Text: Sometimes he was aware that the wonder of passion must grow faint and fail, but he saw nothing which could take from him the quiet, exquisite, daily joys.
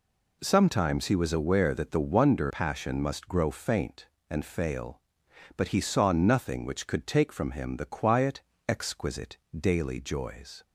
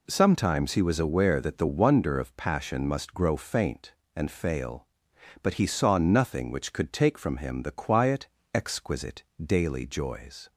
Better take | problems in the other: second | skips "of"; at 2.5 s

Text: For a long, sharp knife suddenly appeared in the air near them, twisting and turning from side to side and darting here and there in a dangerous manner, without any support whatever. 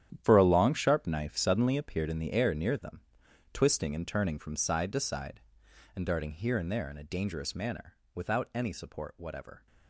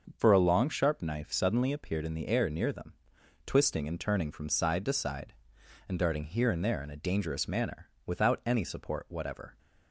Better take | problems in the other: second | gets quieter; strong; throughout; 13 dB // starts louder than the rest; strong; until 1.2 s; 10.5 dB; also in the second

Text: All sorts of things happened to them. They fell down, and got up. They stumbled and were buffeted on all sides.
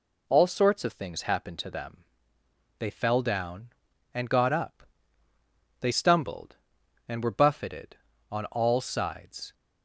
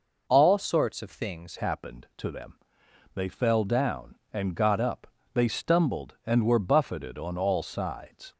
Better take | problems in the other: first | changes voice at "happened"; from 1.5 s on; 6.8 s long

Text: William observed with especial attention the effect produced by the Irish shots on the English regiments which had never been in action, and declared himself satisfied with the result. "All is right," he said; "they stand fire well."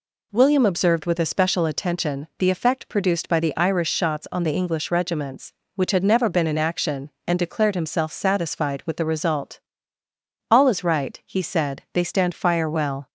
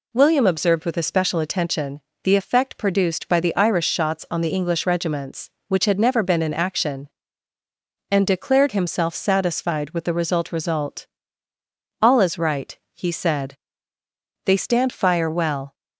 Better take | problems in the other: first | pauses between "attention" and "the"; slight; at 1.9 s; 0.24 s long // says "result" twice; at 10.4 s

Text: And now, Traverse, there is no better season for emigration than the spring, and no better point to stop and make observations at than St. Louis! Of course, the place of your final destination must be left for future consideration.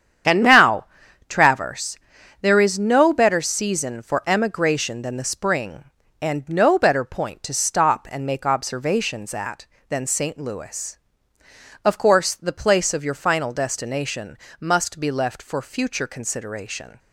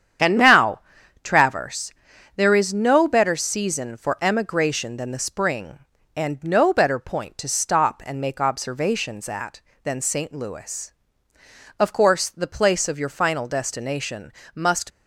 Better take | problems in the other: first | starts louder than the rest; strong; until 1.6 s; 8.5 dB; strong in the first // pauses between "destination" and "must"; slight; at 14.3 s; 0.24 s long; slight in the first // stops before "be left for future consideration"; at 14.9 s

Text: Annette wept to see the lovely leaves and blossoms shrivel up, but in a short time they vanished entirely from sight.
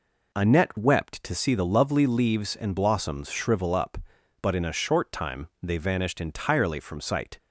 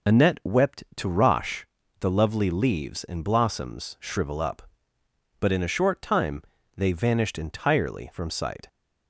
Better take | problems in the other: first | says "rosh" for "see"; at 1.0 s // pauses between "time" and "they"; slight; at 6.4 s; 0.34 s long

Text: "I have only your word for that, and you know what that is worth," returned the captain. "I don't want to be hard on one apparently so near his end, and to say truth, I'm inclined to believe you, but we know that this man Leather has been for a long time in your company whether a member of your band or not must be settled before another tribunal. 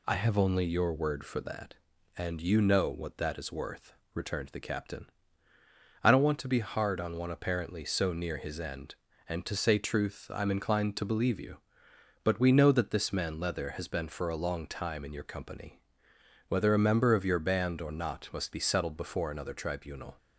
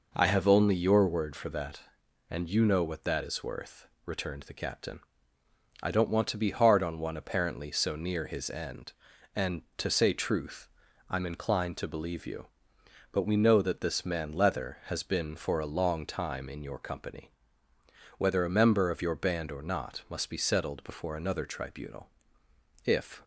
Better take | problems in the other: first | pauses between "company" and "whether"; noticeable; at 17.3 s; 0.88 s long; noticeable in the first // goes on to say "If"; slight; from 22.8 s on; 0.38 s long

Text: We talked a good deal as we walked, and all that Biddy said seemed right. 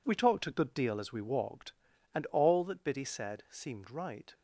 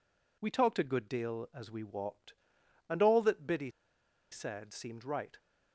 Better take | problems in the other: first | pauses between "Biddy" and "said"; noticeable; at 3.7 s; 0.61 s long

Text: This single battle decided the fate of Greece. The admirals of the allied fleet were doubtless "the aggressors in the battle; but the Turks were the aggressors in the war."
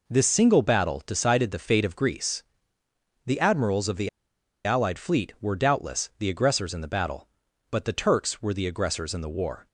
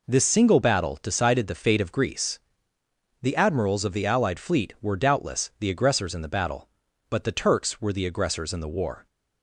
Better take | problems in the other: second | pauses between "the" and "allied"; noticeable; at 4.0 s; 0.57 s long

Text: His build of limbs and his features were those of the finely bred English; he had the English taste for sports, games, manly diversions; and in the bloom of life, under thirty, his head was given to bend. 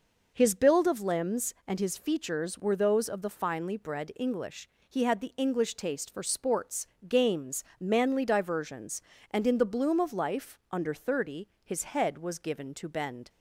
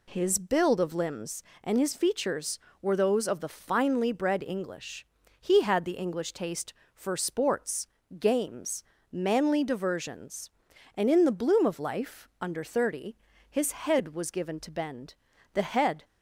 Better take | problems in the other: first | goes on to say "The head"; from 15.5 s on; 0.52 s long

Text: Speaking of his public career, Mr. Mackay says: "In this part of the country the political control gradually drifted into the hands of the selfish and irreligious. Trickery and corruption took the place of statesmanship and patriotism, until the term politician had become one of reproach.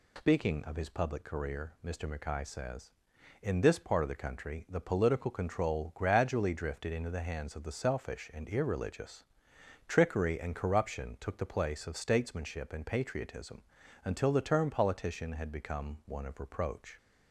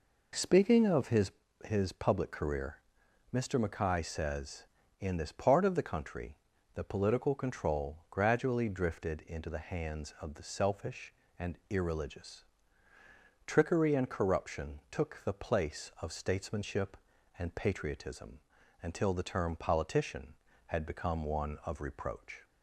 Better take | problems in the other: first | says "his" twice; at 1.6 s // pauses between "country" and "the"; at 6.3 s; 0.40 s long

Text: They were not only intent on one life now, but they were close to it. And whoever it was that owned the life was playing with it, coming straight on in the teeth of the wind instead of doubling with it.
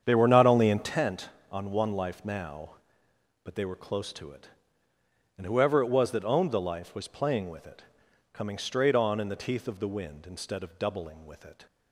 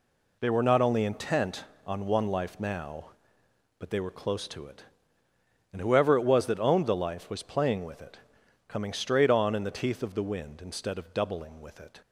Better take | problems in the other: second | starts louder than the rest; strong; until 1.0 s; 8 dB

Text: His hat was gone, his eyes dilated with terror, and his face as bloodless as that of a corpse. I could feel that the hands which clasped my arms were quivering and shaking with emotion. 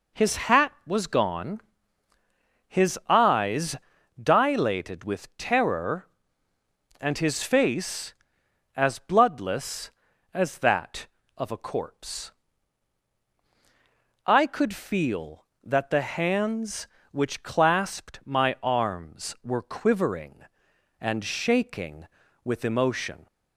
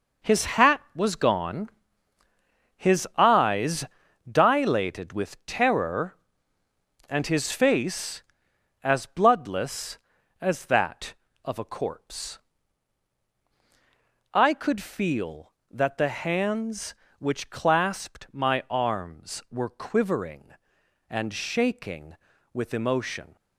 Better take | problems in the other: first | gets quieter; strong; throughout; 9.5 dB // pauses between "eyes" and "dilated"; at 3.8 s; 0.44 s long; also in the first

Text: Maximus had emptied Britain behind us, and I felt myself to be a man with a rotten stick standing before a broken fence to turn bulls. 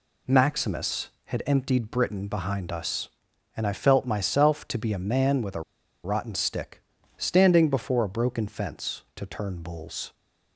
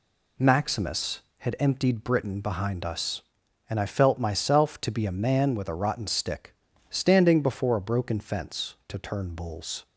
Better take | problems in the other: second | pauses between "a" and "rotten"; at 5.6 s; 0.43 s long // pauses between "stick" and "standing"; slight; at 6.8 s; 0.36 s long; slight in the second

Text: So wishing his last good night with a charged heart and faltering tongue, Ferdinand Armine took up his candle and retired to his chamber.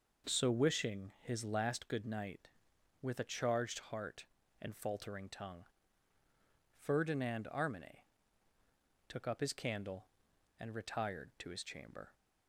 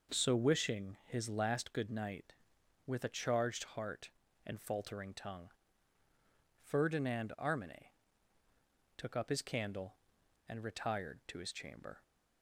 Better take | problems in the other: neither | pauses between "Armine" and "took"; the same in both

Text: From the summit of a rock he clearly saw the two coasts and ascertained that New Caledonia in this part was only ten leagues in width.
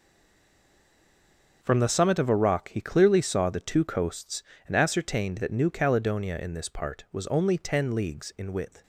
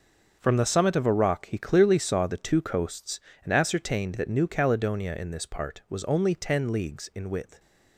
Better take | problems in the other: second | stays silent before the first word; noticeable; until 1.6 s; 1.6 s long // starts louder than the rest; until 2.6 s; 6.5 dB; also in the second

